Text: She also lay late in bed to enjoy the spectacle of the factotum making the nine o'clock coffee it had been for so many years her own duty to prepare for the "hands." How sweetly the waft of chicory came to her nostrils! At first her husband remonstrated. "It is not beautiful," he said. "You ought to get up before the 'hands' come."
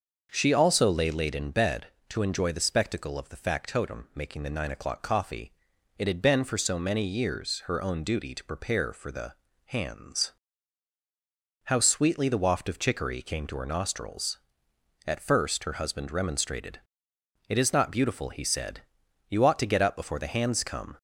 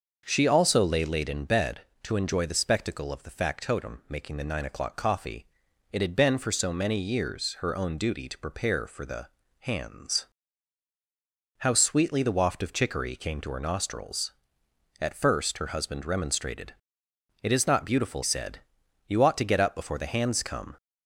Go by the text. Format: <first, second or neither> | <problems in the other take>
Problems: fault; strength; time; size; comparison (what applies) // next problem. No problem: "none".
first | starts louder than the rest; until 1.2 s; 6.5 dB; also in the first // pauses between "coffee" and "it"; noticeable; at 5.4 s; 0.46 s long; noticeable in the first // pauses between "the" and "hands"; slight; at 9.2 s; 0.32 s long; slight in the first // skips "he"; at 18.2 s